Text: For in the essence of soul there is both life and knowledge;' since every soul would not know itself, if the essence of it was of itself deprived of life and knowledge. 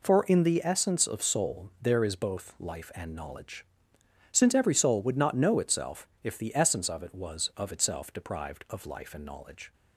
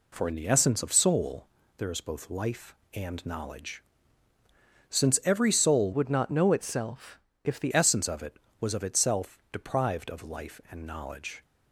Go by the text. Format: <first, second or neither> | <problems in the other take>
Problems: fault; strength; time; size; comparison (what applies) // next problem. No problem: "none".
first | pauses between "soul" and "there"; slight; at 1.4 s; 0.30 s long // changes voice from "would" to "the"; from 5.9 to 7.7 s; 1.8 s long